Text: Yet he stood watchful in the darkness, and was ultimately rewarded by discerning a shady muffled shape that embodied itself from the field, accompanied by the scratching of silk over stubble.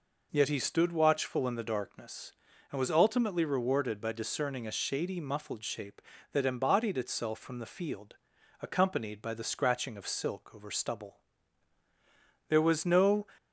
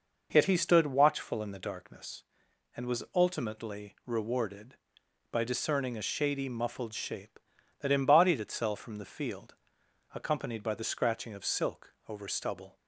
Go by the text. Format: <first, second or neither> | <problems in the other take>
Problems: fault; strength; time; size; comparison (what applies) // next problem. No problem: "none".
second | goes on to say "There was no"; noticeable; from 12.4 s on; 0.78 s long